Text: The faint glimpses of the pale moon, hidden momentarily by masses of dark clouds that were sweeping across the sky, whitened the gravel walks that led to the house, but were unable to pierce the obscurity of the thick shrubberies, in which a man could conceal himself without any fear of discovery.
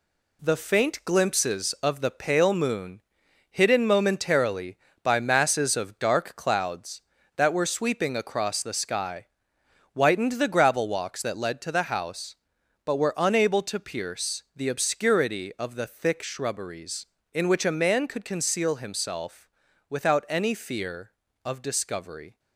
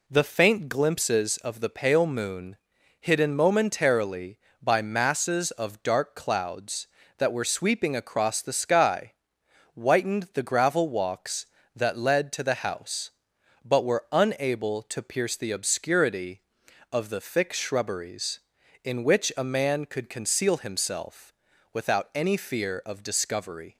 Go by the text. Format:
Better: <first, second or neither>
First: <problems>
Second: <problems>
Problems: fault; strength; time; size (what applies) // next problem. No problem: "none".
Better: second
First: gets quieter; noticeable; throughout; 6 dB // pauses between "himself" and "without"; at 19.4 s; 0.40 s long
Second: pauses between "himself" and "without"; at 21.3 s; 0.40 s long